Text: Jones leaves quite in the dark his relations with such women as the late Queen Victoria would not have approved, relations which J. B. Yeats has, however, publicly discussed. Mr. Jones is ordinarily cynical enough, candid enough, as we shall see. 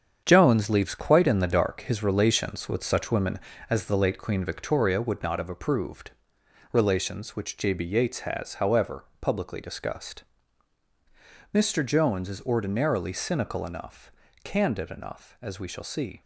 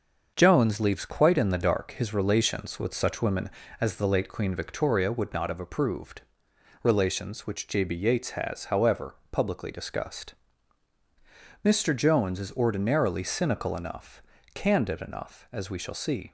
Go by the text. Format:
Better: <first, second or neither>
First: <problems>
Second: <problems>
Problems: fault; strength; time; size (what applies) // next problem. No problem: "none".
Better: second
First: gets quieter; strong; throughout; 8 dB // starts louder than the rest; strong; until 1.2 s; 7.5 dB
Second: starts louder than the rest; until 1.3 s; 6.5 dB